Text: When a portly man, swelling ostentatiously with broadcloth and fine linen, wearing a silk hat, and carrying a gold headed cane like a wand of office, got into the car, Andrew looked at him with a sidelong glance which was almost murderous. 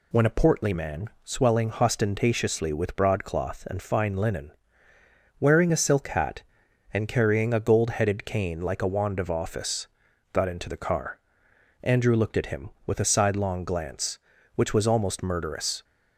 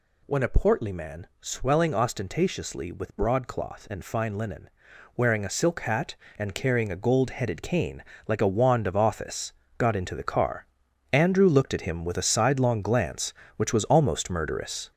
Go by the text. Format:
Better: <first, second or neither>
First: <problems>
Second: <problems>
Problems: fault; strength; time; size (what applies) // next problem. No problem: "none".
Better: first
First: none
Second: gets louder; throughout; 6 dB // pauses between "cane" and "like"; slight; at 8.0 s; 0.24 s long